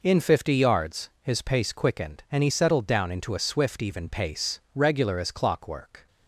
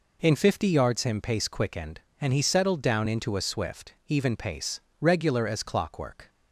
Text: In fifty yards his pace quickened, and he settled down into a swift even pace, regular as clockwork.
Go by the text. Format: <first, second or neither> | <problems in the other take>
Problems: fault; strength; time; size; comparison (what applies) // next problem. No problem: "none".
first | says "him" for "his"; at 1.0 s // pauses between "swift" and "even"; slight; at 3.9 s; 0.16 s long